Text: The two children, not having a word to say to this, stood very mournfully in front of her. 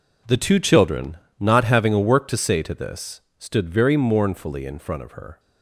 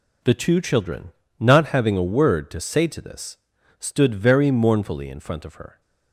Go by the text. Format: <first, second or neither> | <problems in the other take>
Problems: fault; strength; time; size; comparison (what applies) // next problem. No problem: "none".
second | says "work" for "word"; at 1.9 s